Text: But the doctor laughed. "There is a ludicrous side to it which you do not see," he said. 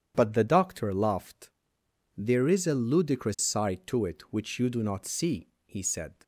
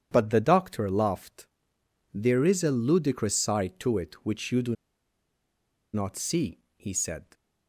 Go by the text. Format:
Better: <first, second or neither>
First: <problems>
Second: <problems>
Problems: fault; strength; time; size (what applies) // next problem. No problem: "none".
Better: first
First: none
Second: pauses between "do" and "not"; at 4.7 s; 1.1 s long